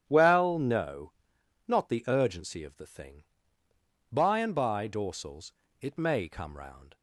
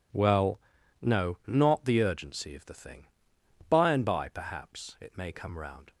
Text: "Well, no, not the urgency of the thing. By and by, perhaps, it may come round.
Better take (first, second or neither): second